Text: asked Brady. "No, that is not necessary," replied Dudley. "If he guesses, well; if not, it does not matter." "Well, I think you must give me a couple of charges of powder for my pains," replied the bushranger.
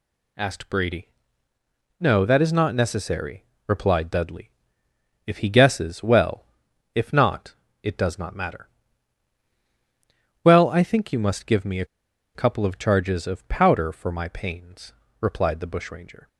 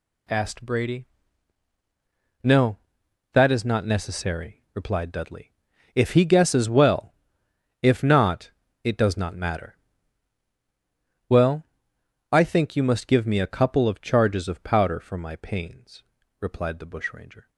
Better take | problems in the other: second | pauses between "a" and "couple"; noticeable; at 11.8 s; 0.49 s long

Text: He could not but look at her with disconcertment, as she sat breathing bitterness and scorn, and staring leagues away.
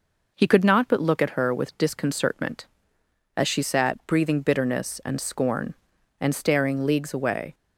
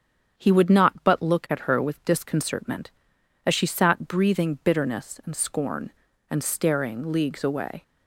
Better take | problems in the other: first | starts louder than the rest; strong; until 1.4 s; 7.5 dB // says "would" for "could"; at 0.5 s

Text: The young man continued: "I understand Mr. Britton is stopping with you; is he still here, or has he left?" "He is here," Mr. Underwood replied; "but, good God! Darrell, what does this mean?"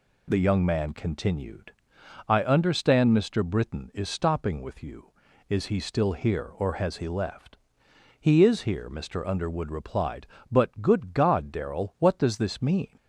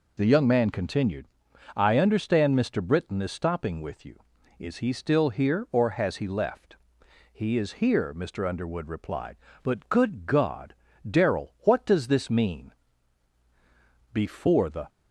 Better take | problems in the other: first | goes on to say "Before the"; noticeable; from 14.1 s on; 0.76 s long

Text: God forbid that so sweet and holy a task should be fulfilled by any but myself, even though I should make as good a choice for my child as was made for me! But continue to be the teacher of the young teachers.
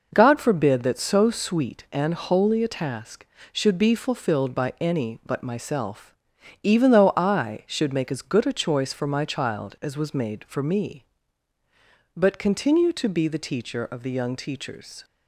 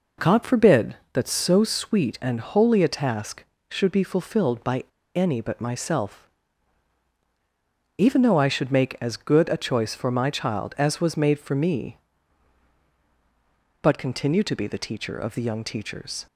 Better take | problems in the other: first | pauses between "by" and "any"; slight; at 4.8 s; 0.32 s long

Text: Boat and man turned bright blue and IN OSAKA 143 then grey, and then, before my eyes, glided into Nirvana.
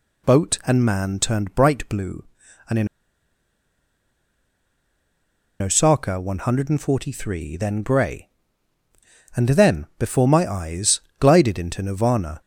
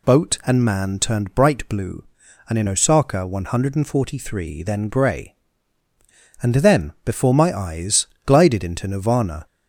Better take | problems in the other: second | pauses between "IN" and "OSAKA"; strong; at 2.8 s; 2.7 s long

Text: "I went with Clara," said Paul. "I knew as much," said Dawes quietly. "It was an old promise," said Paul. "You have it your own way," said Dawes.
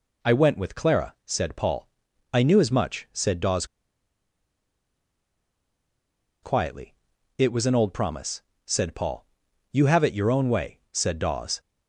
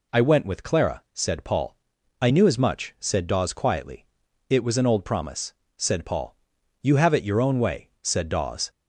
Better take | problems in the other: second | pauses between "Dawes" and "quietly"; strong; at 3.6 s; 2.7 s long

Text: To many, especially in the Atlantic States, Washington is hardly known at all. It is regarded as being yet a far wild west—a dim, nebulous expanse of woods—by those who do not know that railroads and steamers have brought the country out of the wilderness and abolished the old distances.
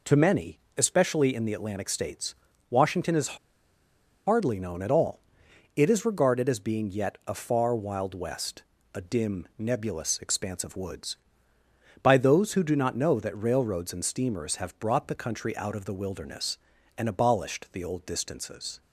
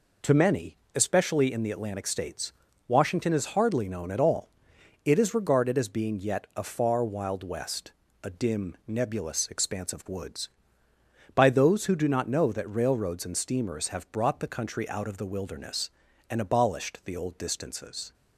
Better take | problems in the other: second | pauses between "is" and "hardly"; noticeable; at 3.3 s; 0.90 s long

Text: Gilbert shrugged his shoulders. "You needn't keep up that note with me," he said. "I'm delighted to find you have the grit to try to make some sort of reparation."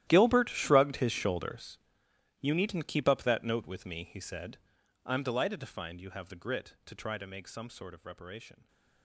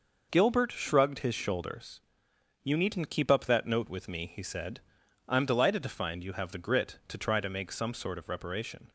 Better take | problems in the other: second | gets quieter; strong; throughout; 18.5 dB

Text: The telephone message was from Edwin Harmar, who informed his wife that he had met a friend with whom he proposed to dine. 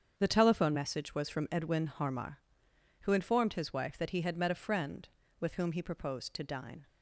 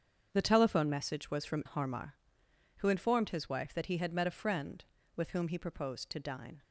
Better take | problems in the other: first | starts louder than the rest; strong; until 1.3 s; 7.5 dB; strong in the first // skips "Edwin"; at 1.6 s

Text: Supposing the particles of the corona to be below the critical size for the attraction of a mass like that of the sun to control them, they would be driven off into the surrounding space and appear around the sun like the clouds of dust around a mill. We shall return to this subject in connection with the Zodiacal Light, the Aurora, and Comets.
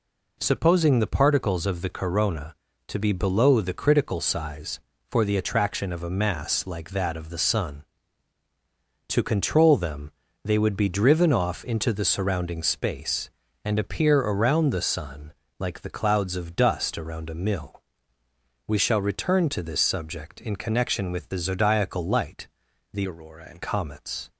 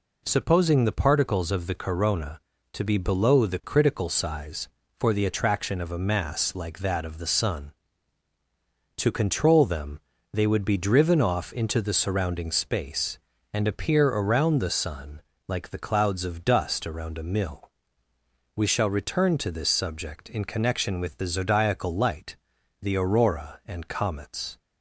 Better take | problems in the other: second | pauses between "sun" and "like"; slight; at 15.3 s; 0.24 s long; slight in the second // changes voice from "Aurora" to "and"; from 23.0 to 23.6 s; 0.6 s long

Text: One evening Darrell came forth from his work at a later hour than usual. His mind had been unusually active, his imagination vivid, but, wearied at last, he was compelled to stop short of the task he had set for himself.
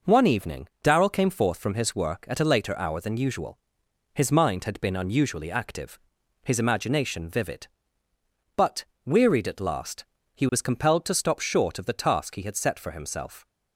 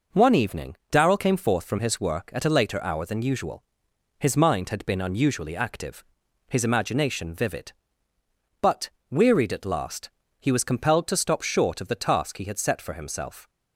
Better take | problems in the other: neither | pauses between "evening" and "Darrell"; slight; the same in both

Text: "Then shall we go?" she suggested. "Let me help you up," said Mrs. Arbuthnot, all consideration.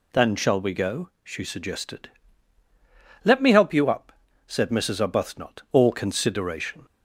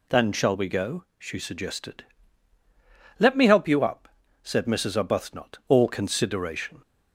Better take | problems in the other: neither | none

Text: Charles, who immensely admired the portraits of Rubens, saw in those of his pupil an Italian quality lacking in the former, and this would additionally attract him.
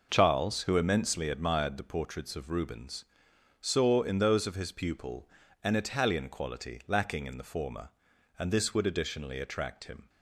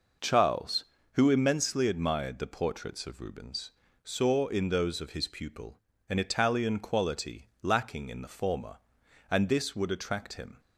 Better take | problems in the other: first | pauses between "pupil" and "an"; slight; at 5.7 s; 0.30 s long; slight in the first // skips "additionally"; at 9.9 s

